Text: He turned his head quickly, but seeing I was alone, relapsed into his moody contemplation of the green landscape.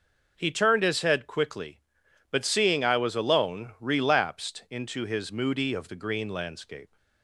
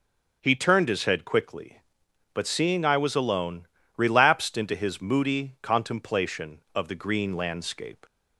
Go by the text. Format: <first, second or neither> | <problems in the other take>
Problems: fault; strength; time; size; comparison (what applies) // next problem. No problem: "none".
second | skips "contemplation"; at 5.7 s